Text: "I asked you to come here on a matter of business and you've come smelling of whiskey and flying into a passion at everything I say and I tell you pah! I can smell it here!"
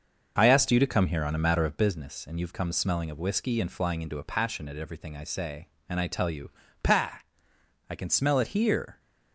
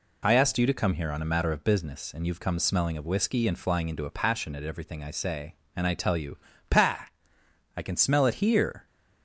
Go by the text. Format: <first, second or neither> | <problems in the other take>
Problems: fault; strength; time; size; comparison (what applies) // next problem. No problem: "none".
second | starts louder than the rest; noticeable; until 1.9 s; 6 dB // pauses between "you" and "pah"; slight; at 6.5 s; 0.32 s long; slight in the second